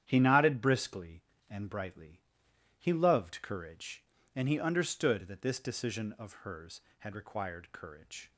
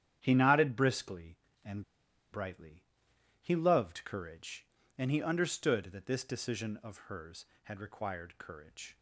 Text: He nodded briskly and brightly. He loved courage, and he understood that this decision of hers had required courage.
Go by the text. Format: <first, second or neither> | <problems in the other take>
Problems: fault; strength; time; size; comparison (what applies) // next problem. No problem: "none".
first | starts louder than the rest; strong; until 1.2 s; 10 dB; strong in the first // pauses between "and" and "brightly"; noticeable; at 1.8 s; 0.50 s long